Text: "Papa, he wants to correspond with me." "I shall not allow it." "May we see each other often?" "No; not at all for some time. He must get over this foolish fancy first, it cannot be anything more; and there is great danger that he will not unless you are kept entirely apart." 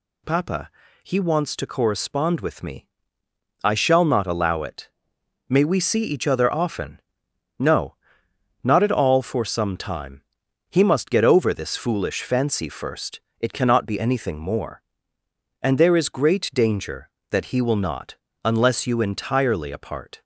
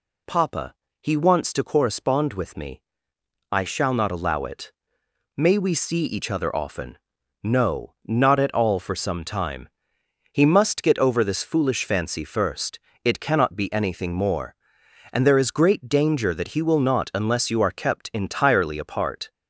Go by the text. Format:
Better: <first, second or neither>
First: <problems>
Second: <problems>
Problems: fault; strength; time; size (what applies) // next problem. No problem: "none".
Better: second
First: pauses between "not" and "unless"; slight; at 18.1 s; 0.28 s long // skips "are kept"; at 19.0 s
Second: none